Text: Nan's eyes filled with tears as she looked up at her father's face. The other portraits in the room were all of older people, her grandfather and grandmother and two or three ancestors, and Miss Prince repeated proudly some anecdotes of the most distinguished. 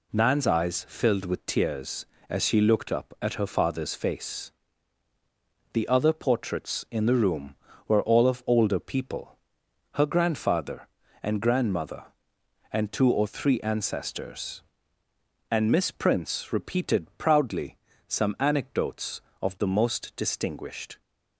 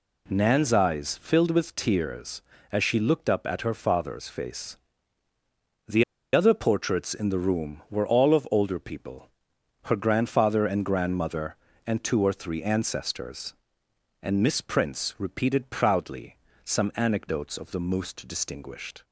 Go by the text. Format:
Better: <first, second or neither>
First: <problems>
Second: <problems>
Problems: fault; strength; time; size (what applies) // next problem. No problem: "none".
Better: first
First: pauses between "proudly" and "some"; slight; at 17.7 s; 0.30 s long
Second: pauses between "The" and "other"; slight; at 6.0 s; 0.30 s long // pauses between "proudly" and "some"; slight; at 16.3 s; 0.26 s long